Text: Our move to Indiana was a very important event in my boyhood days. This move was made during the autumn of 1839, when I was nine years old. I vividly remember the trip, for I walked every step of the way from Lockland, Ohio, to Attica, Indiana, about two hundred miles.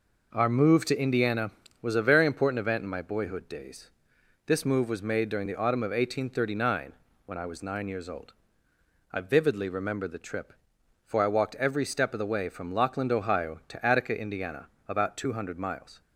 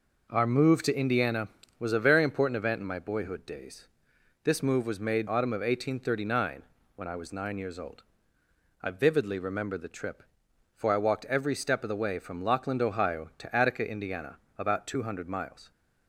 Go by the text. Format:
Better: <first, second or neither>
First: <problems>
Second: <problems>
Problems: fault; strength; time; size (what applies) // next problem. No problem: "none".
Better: first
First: none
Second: skips "during the"; at 5.2 s